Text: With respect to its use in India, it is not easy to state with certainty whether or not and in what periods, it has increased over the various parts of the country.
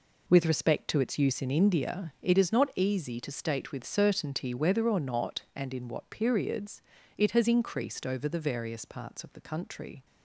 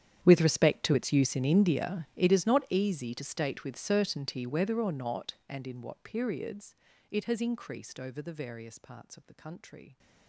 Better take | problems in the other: first | gets quieter; strong; throughout; 21 dB

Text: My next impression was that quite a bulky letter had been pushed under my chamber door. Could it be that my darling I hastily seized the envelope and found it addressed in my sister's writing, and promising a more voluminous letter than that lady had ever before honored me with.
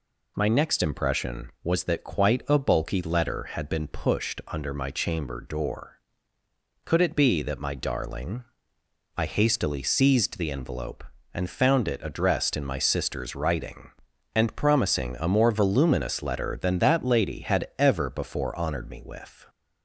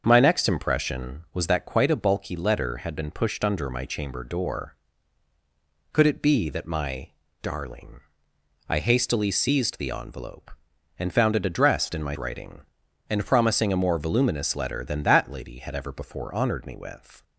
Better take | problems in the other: first | starts louder than the rest; until 1.0 s; 6.5 dB // pauses between "my" and "darling"; slight; at 7.0 s; 0.32 s long // pauses between "darling" and "I"; noticeable; at 8.0 s; 0.68 s long; noticeable in the first // skips "sister's"; at 12.1 s

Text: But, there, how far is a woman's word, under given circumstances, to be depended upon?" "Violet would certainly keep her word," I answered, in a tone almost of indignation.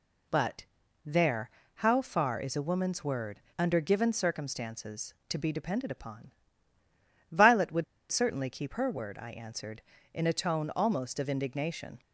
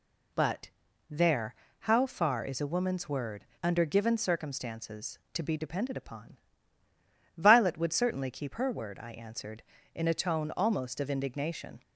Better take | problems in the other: second | pauses between "would" and "certainly"; slight; at 7.8 s; 0.25 s long

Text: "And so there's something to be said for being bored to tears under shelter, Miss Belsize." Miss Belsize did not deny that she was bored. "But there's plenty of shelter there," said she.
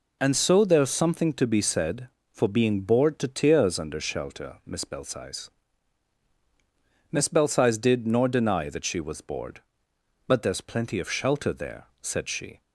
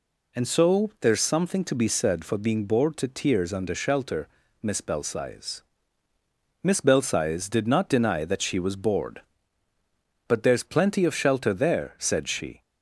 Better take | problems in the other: second | says "nor" for "not"; at 8.0 s

